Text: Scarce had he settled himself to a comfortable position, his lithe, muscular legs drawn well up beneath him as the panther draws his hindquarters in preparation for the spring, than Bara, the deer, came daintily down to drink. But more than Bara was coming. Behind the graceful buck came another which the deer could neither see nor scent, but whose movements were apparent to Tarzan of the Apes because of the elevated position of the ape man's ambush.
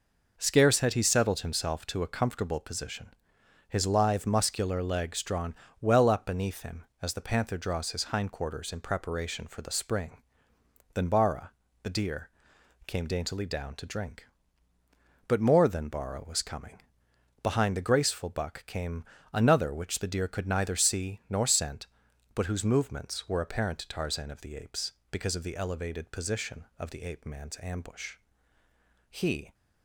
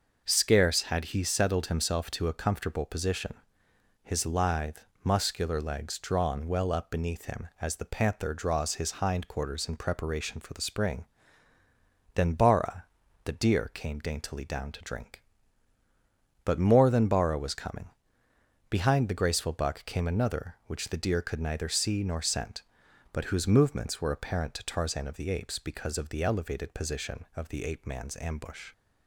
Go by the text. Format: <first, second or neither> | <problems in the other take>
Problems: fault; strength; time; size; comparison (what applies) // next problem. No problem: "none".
second | pauses between "drawn" and "well"; slight; at 5.5 s; 0.26 s long // pauses between "came" and "another"; slight; at 19.0 s; 0.28 s long // goes on to say "He"; slight; from 29.0 s on; 0.44 s long